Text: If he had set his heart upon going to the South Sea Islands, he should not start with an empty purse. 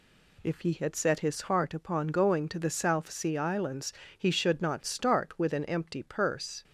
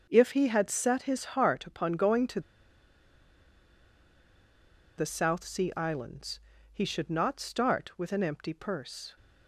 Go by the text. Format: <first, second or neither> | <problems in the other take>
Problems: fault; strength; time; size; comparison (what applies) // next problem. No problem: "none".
first | starts louder than the rest; until 1.0 s; 6.5 dB // pauses between "to" and "the"; strong; at 2.4 s; 2.5 s long